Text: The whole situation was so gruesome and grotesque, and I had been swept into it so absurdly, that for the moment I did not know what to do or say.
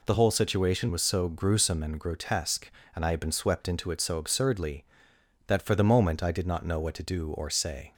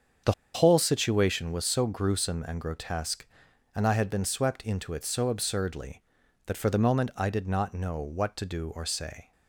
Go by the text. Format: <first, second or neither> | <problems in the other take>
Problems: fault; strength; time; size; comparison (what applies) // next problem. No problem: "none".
first | starts louder than the rest; strong; until 1.4 s; 7 dB // pauses between "The" and "whole"; slight; at 0.3 s; 0.20 s long